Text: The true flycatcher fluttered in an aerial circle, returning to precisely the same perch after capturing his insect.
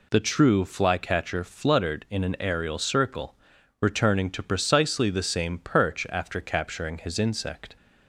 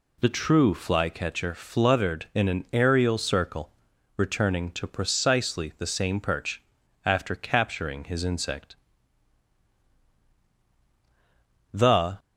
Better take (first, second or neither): first